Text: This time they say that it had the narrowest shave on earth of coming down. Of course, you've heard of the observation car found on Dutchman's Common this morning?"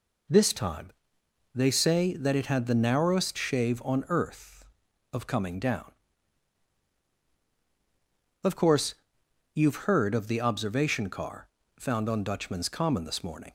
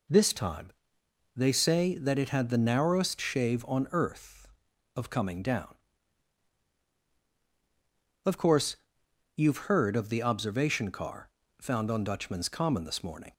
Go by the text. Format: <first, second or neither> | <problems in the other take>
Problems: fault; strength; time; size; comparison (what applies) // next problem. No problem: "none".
neither | pauses between "time" and "they"; noticeable; the same in both // pauses between "car" and "found"; slight; the same in both